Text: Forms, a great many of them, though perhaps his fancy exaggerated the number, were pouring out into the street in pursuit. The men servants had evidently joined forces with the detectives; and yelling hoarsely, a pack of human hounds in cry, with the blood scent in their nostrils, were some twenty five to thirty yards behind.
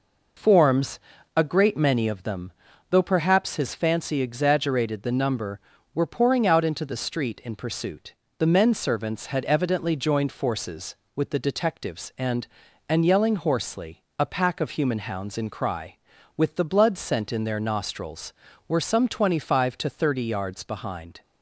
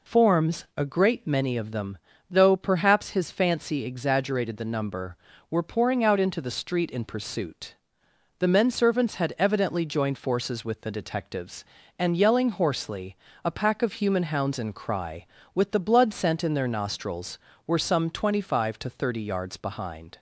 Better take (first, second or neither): second